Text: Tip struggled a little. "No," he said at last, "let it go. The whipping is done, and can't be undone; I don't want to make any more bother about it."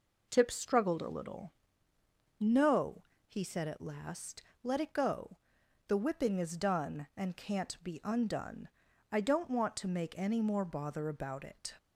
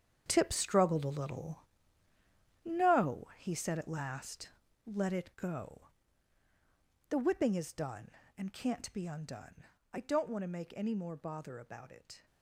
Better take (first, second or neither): first